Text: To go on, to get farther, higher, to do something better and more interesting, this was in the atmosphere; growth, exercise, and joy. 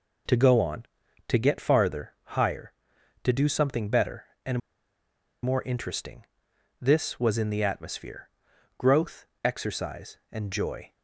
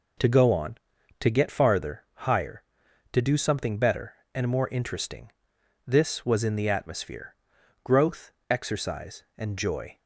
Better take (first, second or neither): second